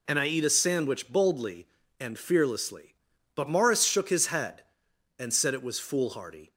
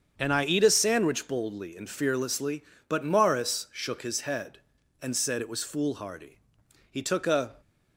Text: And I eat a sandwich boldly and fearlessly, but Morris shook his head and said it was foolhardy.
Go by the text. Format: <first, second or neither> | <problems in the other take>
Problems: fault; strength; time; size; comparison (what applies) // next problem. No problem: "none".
first | starts louder than the rest; strong; until 1.1 s; 7 dB // goes on to say "He took a"; noticeable; from 6.9 s on; 0.70 s long